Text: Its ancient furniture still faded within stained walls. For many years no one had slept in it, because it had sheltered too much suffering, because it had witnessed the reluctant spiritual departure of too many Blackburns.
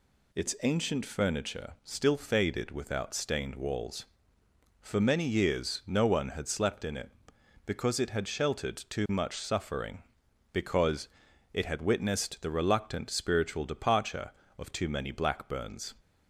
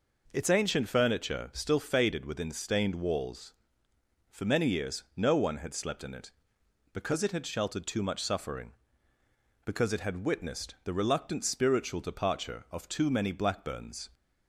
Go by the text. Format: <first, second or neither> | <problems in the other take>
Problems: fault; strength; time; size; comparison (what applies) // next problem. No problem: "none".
second | says "without" for "within"; at 2.7 s // pauses between "because" and "it"; noticeable; at 11.0 s; 0.46 s long